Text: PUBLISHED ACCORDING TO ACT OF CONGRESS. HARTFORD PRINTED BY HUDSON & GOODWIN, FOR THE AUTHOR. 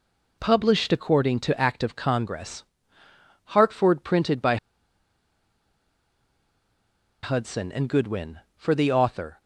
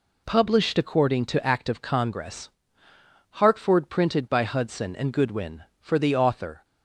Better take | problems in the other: second | pauses between "BY" and "HUDSON"; strong; at 4.5 s; 2.6 s long

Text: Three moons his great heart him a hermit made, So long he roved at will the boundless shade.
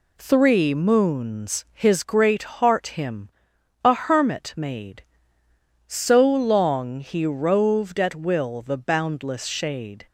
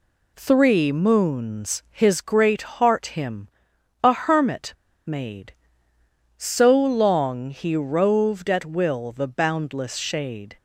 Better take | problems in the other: first | pauses between "him" and "a"; noticeable; at 3.4 s; 0.54 s long; noticeable in the first // pauses between "hermit" and "made"; slight; at 4.7 s; 0.34 s long

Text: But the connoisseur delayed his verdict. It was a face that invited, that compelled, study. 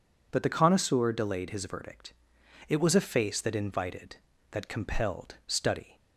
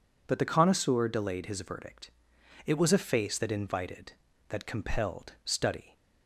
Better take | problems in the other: neither | none

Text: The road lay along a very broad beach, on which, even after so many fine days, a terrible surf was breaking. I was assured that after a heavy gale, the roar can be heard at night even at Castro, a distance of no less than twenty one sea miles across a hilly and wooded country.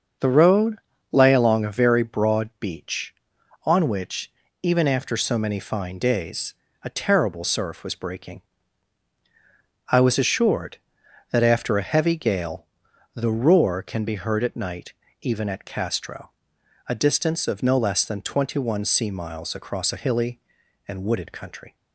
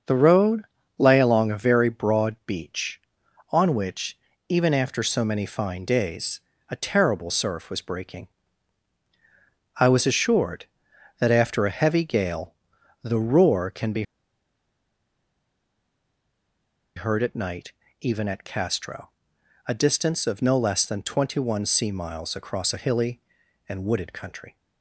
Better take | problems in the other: first | starts louder than the rest; until 1.4 s; 6.5 dB; also in the first // pauses between "road" and "lay"; slight; at 0.6 s; 0.36 s long; slight in the first // pauses between "be" and "heard"; strong; at 14.0 s; 2.9 s long // pauses between "night" and "even"; slight; at 17.7 s; 0.28 s long; slight in the first

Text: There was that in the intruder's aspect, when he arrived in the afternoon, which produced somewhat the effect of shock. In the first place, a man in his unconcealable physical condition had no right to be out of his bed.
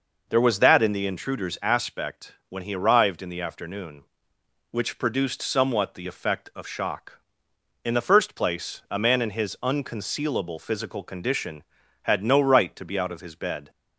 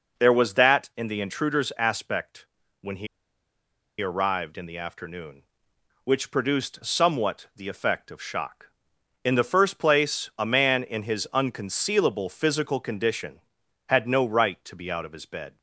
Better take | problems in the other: first | pauses between "he" and "arrived"; noticeable; at 3.0 s; 0.94 s long

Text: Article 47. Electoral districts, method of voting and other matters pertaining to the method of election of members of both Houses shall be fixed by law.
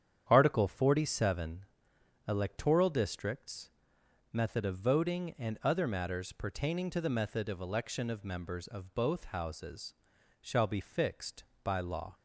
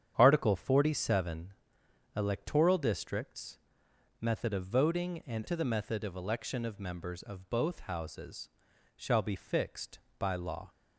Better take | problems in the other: first | starts louder than the rest; strong; until 1.1 s; 9 dB; strong in the first // skips "other matters pertaining"; at 5.4 s // pauses between "Houses" and "shall"; noticeable; at 8.4 s; 0.48 s long; noticeable in the first

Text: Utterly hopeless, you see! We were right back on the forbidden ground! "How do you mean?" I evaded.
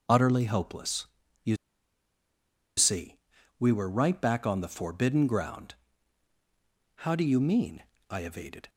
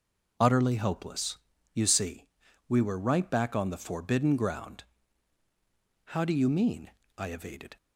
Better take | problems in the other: second | pauses between "you" and "see"; at 1.5 s; 1.2 s long

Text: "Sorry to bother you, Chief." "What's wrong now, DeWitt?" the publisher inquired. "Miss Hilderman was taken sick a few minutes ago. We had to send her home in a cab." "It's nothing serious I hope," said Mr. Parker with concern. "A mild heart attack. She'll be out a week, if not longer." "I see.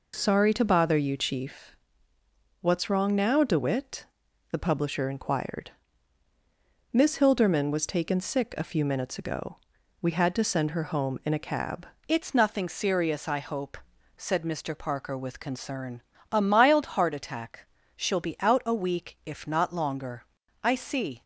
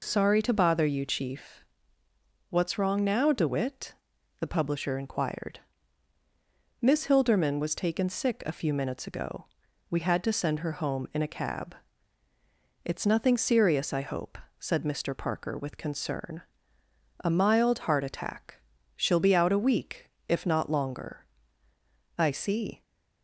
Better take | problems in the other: second | changes voice at "It's"; from 12.0 s on; 9.2 s long

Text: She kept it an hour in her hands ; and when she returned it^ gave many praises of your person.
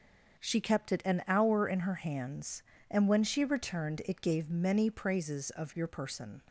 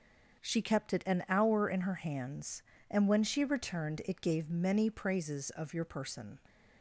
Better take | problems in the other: neither | starts louder than the rest; the same in both

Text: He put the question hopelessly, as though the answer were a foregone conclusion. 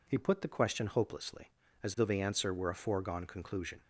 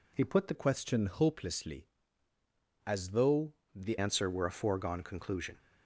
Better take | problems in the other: first | changes voice from "question" to "the"; from 0.5 to 3.9 s; 3.4 s long // pauses between "though" and "the"; slight; at 3.5 s; 0.20 s long

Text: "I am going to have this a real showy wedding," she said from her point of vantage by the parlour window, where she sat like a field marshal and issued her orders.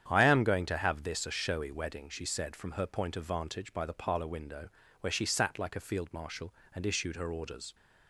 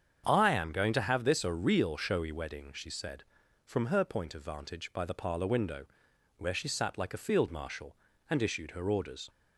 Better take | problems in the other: second | starts louder than the rest; strong; until 1.1 s; 9 dB; strong in the second // skips "real"; at 1.3 s

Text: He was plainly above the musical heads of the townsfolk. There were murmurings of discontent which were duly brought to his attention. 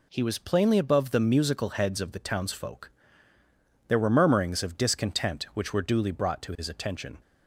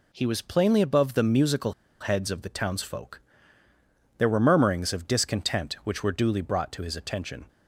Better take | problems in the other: first | pauses between "musical" and "heads"; slight; at 1.7 s; 0.26 s long

